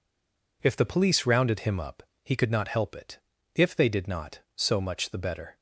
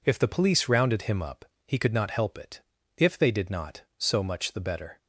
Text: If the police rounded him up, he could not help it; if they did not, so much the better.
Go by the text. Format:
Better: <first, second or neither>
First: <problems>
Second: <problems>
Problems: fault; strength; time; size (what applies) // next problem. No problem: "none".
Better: second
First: stays silent before the first word; slight; until 0.6 s; 0.6 s long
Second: none